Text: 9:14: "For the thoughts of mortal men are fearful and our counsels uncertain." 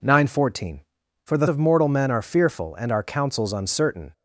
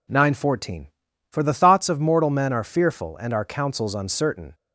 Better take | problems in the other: second | skips "thoughts"; at 1.4 s

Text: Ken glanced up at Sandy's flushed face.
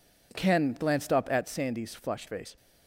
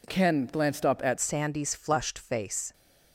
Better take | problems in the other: first | changes voice at "Sandy's"; from 1.1 s on; 1.6 s long

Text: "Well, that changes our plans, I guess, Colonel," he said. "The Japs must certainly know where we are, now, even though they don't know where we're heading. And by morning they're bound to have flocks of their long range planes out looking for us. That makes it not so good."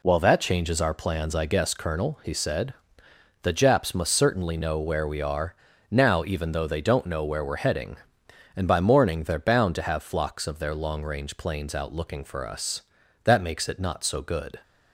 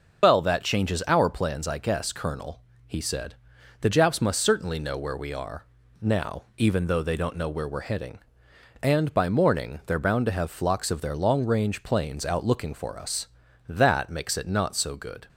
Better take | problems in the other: first | loses the start of "Well"; at 0.2 s; 110 ms

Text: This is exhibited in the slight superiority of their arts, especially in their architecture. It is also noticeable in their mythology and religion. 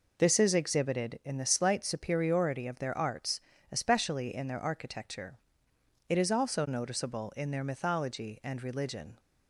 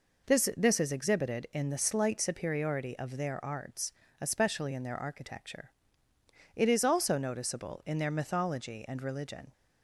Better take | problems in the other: first | says "This" twice; at 0.5 s

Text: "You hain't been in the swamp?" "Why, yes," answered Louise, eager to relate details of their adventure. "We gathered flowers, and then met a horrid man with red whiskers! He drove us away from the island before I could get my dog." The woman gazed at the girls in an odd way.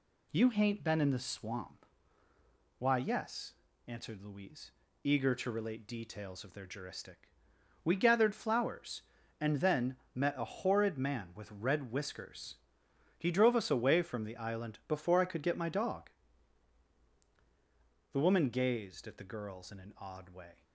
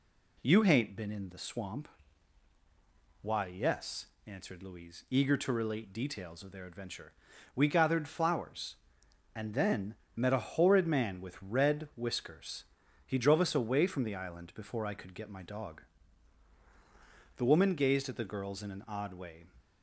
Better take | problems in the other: second | says "juristic" for "adventure"; at 6.6 s // pauses between "then" and "met"; slight; at 9.9 s; 0.16 s long; slight in the second

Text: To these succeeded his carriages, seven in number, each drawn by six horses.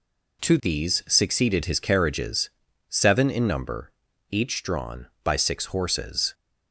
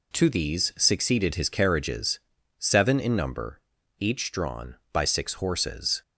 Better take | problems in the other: neither | none

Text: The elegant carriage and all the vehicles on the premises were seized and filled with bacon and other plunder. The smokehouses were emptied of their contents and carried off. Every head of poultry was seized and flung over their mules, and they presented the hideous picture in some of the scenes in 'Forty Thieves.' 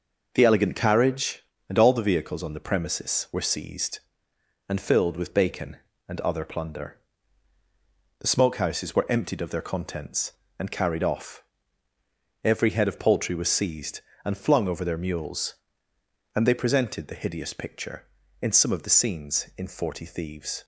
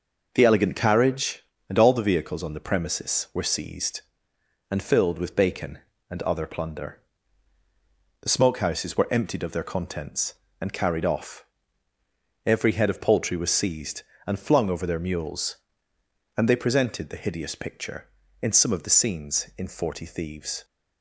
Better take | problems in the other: neither | none

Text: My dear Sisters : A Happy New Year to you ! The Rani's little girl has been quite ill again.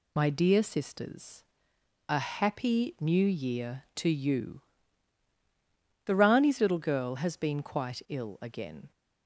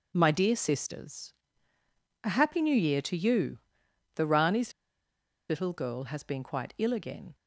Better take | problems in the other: first | pauses between "Rani's" and "little"; noticeable; at 4.7 s; 0.78 s long

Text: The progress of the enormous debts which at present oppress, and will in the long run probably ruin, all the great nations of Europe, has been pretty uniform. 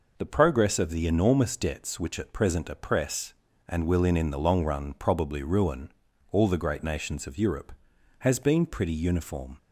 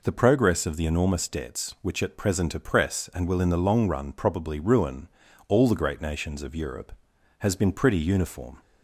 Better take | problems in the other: second | says "in" twice; at 4.1 s

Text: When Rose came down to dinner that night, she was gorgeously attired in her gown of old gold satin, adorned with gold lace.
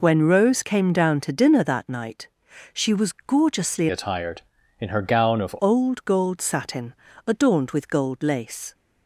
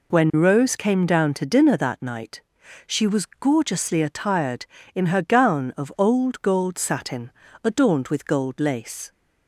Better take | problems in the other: second | changes voice from "attired" to "of"; from 3.8 to 5.5 s; 1.7 s long

